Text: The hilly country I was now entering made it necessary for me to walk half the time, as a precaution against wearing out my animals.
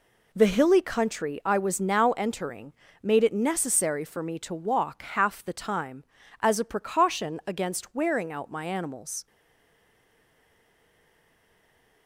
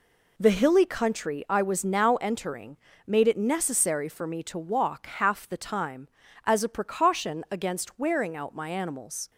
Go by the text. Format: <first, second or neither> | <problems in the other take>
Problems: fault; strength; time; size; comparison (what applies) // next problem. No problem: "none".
second | pauses between "entering" and "made"; slight; at 2.7 s; 0.30 s long; slight in the second // stays silent after the last word; strong; from 9.2 s on; 2.8 s long